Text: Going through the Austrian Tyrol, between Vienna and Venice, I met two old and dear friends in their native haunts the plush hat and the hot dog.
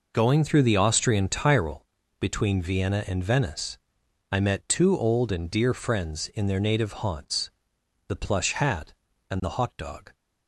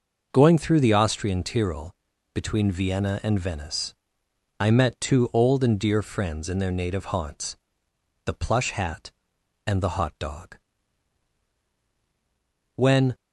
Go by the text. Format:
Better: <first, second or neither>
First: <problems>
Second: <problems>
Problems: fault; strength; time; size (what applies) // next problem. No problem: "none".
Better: first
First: pauses between "haunts" and "the"; noticeable; at 7.4 s; 0.60 s long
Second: pauses between "haunts" and "the"; noticeable; at 7.5 s; 0.68 s long // goes on to say "When"; slight; from 12.7 s on; 0.40 s long